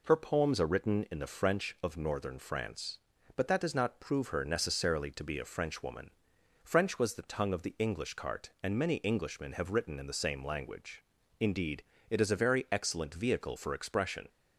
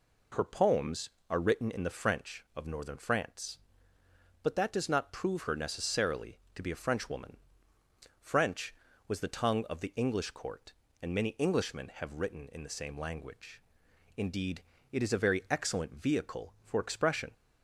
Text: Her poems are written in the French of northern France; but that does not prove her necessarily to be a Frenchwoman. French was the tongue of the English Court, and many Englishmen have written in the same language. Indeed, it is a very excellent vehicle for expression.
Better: second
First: says "Cart" for "Court"; at 8.1 s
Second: none

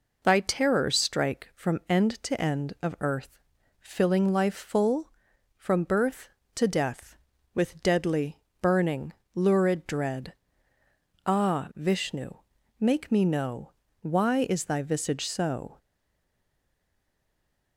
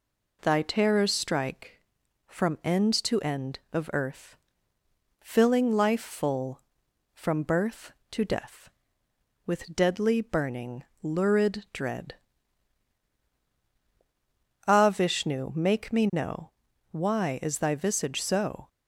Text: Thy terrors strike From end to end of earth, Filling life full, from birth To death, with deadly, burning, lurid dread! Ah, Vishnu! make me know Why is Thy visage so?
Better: second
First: pauses between "know" and "Why"; slight; at 13.7 s; 0.30 s long // stays silent after the last word; noticeable; from 15.7 s on; 2.0 s long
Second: pauses between "know" and "Why"; at 16.4 s; 0.40 s long

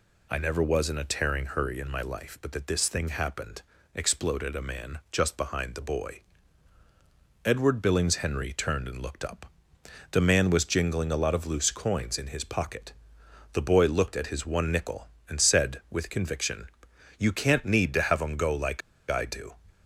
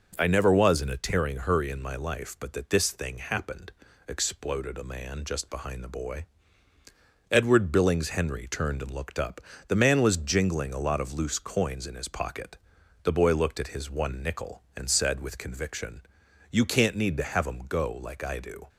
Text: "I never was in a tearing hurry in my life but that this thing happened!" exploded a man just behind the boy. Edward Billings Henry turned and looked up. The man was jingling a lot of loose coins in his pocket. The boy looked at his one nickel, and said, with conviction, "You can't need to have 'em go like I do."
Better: second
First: pauses between "like" and "I"; slight; at 18.8 s; 0.28 s long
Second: none

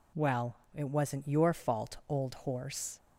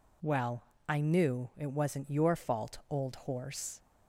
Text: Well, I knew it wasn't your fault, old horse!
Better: second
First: skips "I knew"; at 0.6 s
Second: none

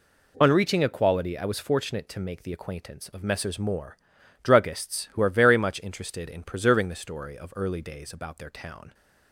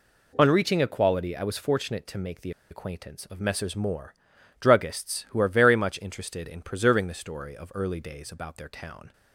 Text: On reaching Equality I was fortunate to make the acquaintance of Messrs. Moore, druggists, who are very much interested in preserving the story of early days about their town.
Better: first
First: none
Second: pauses between "the" and "acquaintance"; slight; at 2.5 s; 0.19 s long

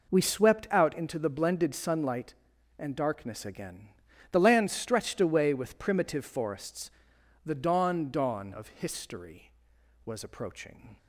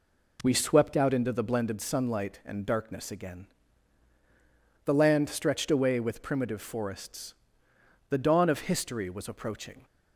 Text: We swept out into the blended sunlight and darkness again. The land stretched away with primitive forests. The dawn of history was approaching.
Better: second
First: says "dawn" twice; at 8.0 s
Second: none

